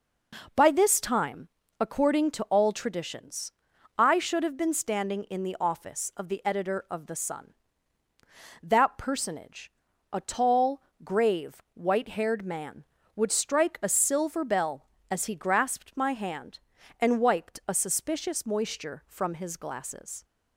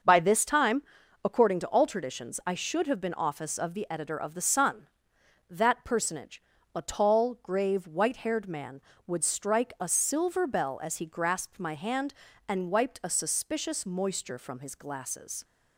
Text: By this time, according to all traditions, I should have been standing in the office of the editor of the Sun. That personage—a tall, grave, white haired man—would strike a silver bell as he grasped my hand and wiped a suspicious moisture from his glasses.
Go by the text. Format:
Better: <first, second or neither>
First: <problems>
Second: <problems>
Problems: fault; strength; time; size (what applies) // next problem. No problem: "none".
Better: first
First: none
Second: starts louder than the rest; until 1.4 s; 6.5 dB // skips "standing in the"; at 3.1 s